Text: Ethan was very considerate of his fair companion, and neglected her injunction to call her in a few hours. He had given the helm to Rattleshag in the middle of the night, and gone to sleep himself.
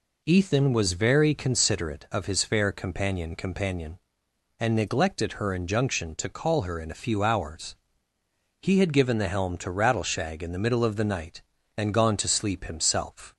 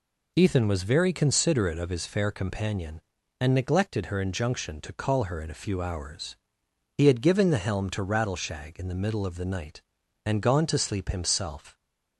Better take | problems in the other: second | says "companion" twice; at 3.3 s

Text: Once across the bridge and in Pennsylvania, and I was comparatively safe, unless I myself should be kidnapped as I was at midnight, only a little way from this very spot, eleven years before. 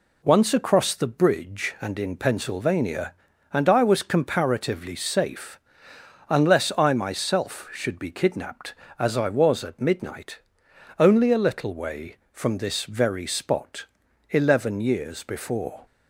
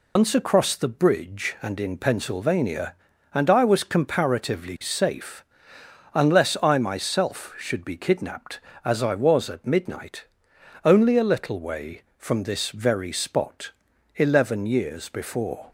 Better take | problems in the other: first | loses the start of "Once"; at 0.1 s; 100 ms

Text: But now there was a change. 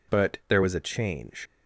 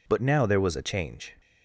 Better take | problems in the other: second | skips "now"; at 0.4 s

